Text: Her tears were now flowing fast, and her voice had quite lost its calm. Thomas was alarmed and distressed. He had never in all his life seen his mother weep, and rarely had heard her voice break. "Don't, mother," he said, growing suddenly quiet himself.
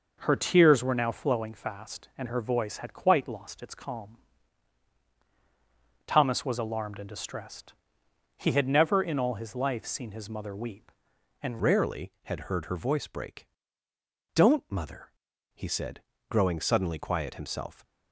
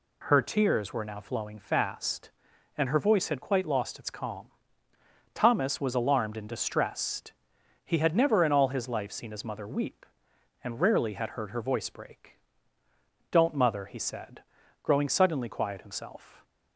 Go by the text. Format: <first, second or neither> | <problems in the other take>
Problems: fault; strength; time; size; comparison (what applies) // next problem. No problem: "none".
second | changes voice at "rarely"; from 11.6 s on; 6.2 s long